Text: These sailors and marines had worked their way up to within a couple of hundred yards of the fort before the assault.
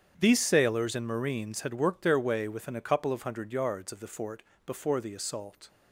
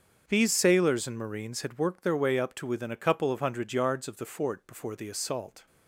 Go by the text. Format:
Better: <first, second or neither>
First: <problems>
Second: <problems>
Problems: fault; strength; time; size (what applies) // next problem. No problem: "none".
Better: second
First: starts louder than the rest; strong; until 1.1 s; 8.5 dB // skips "up to"; at 2.4 s // pauses between "fort" and "before"; slight; at 4.4 s; 0.22 s long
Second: starts louder than the rest; until 1.2 s; 7 dB